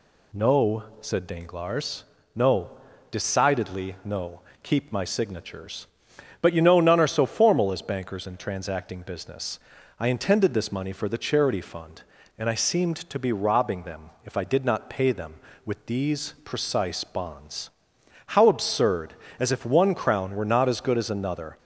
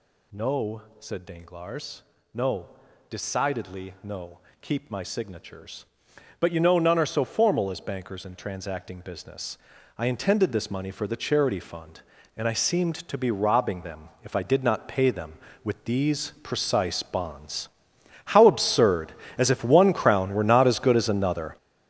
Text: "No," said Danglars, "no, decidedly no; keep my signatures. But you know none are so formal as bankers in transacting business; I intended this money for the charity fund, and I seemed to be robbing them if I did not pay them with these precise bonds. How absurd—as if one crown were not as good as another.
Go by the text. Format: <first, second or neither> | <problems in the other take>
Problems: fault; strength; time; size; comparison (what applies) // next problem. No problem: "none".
first | gets louder; strong; throughout; 11.5 dB // pauses between "them" and "if"; slight; at 14.0 s; 0.16 s long; slight in the first